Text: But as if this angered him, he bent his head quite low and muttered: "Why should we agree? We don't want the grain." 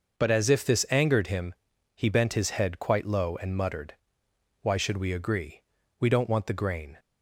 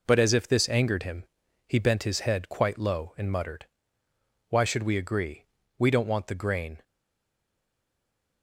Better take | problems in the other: first | stays silent after the last word; noticeable; from 6.8 s on; 1.6 s long

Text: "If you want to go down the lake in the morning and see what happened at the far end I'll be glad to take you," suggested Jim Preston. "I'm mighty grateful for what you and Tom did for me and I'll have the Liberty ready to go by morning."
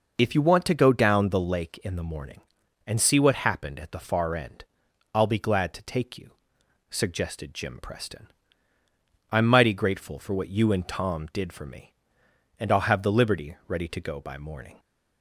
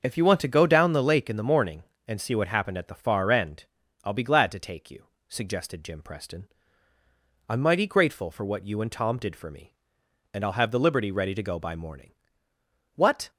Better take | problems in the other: first | starts louder than the rest; until 1.0 s; 6 dB // pauses between "end" and "I'll"; at 3.6 s; 0.40 s long; noticeable in the first // goes on to say "What"; slight; from 12.9 s on; 0.36 s long

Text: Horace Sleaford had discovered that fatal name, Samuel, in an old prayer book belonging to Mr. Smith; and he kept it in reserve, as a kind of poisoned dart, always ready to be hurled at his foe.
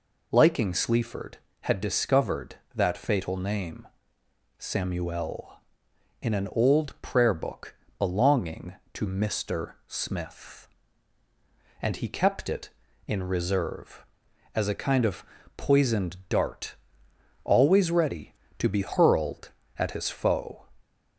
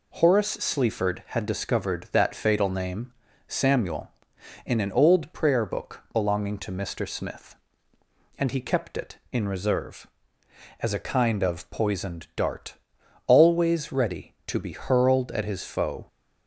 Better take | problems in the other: second | says "Liking" for "Horace"; at 0.3 s // pauses between "book" and "belonging"; slight; at 7.7 s; 0.24 s long // pauses between "of" and "poisoned"; slight; at 15.2 s; 0.32 s long

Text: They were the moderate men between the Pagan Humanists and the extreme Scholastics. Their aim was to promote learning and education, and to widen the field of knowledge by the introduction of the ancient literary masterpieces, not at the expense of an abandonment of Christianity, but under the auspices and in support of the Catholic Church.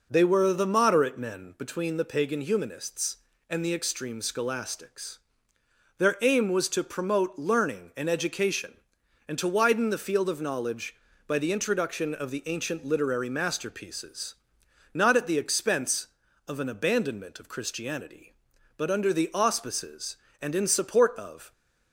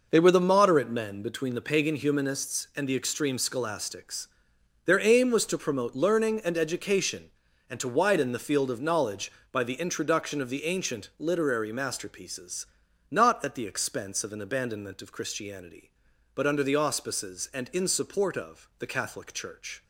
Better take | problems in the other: second | stops before "the Catholic Church"; at 21.5 s

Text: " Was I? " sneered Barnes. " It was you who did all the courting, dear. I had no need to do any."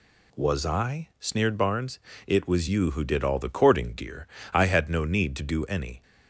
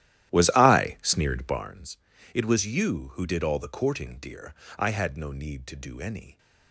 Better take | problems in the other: first | starts louder than the rest; strong; until 1.8 s; 13 dB

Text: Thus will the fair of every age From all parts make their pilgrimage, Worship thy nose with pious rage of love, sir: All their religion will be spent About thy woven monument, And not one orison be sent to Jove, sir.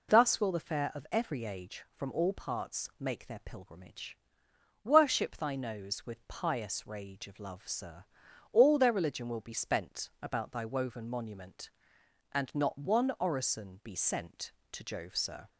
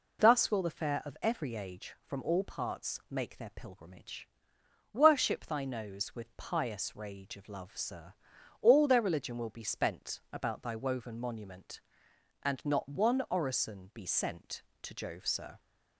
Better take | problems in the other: neither | none

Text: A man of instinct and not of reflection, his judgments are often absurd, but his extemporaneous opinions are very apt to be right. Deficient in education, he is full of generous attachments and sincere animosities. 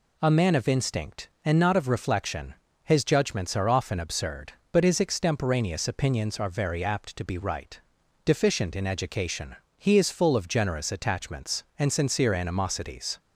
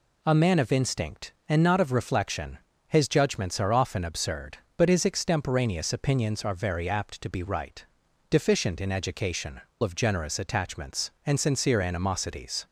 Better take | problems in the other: first | skips "he is full"; at 9.7 s

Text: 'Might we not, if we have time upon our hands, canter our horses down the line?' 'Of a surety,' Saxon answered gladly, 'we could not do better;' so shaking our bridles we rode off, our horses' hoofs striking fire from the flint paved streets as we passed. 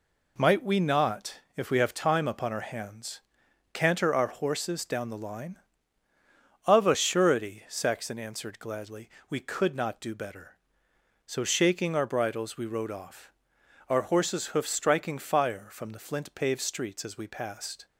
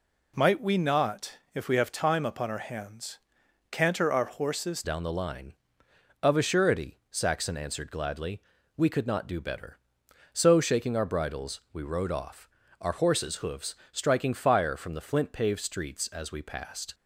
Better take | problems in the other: first | changes voice at "down"; from 4.8 s on; 12.1 s long // pauses between "hoofs" and "striking"; slight; at 13.7 s; 0.18 s long

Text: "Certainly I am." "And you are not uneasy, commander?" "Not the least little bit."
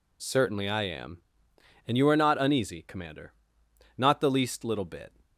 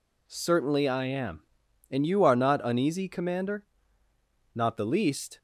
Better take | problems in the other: first | stops before "little bit"; at 5.3 s

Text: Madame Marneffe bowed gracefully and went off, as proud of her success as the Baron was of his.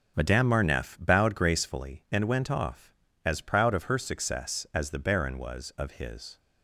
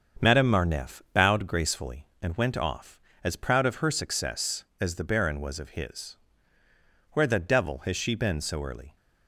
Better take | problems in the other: first | starts louder than the rest; strong; until 1.3 s; 7 dB; also in the first // goes on to say "Where the devil has she been so early"; strong; from 7.1 s on; 1.8 s long

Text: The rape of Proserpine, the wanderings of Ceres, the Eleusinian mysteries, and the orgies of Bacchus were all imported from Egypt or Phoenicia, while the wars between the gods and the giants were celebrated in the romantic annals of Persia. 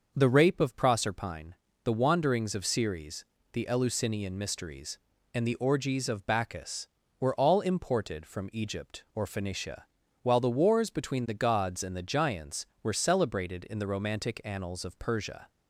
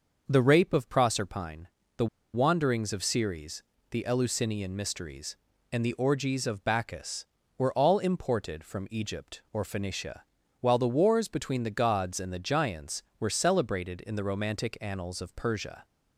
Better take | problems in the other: first | starts louder than the rest; until 1.2 s; 6 dB; also in the first // pauses between "the" and "wanderings"; slight; at 2.0 s; 0.27 s long

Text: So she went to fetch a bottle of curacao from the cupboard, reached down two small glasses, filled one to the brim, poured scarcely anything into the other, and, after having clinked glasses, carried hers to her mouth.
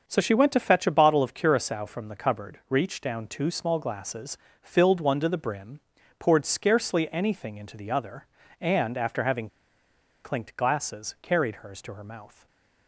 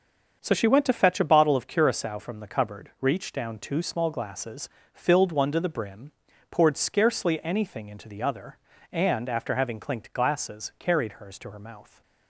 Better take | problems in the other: second | starts louder than the rest; until 1.0 s; 6.5 dB; also in the second // pauses between "having" and "clinked"; noticeable; at 9.4 s; 0.76 s long // stays silent after the last word; slight; from 12.3 s on; 0.5 s long

